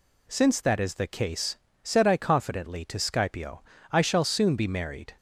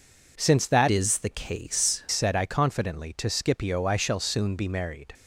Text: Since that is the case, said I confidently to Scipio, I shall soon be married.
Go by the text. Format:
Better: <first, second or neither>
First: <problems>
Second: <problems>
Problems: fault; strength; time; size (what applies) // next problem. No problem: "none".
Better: first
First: none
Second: changes voice from "is" to "case"; from 0.9 to 2.0 s; 1.1 s long